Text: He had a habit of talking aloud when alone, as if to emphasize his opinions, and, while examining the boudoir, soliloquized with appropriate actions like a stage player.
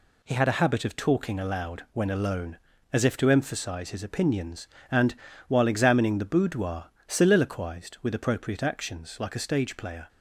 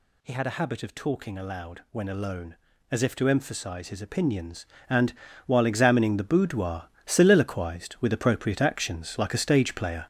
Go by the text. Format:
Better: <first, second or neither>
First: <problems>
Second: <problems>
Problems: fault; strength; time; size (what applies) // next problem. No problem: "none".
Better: first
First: none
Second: gets louder; throughout; 7 dB